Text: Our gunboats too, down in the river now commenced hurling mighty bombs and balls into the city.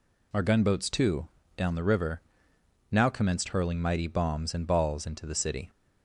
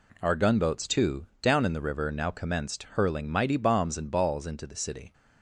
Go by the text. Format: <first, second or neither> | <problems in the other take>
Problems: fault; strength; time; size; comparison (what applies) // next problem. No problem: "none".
second | skips "in"; at 1.7 s // pauses between "river" and "now"; noticeable; at 2.1 s; 0.70 s long